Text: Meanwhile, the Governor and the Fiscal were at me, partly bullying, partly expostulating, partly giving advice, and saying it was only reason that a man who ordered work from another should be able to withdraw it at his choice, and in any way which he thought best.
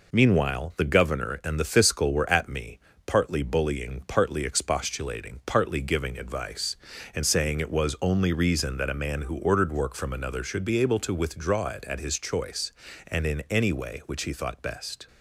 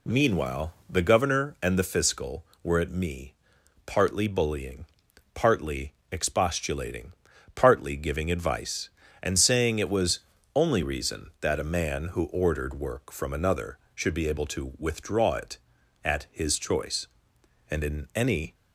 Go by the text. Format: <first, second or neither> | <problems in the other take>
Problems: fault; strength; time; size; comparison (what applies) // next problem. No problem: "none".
first | pauses between "partly" and "expostulating"; slight; at 5.9 s; 0.22 s long // pauses between "was" and "only"; slight; at 10.1 s; 0.36 s long // stops before "way which he thought best"; at 18.5 s